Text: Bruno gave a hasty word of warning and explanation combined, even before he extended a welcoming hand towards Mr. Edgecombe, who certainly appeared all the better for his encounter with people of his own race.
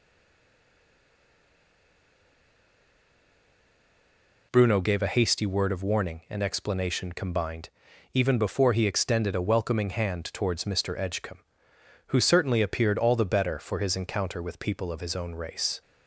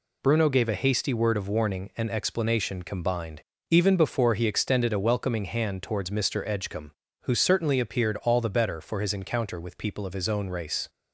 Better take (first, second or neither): second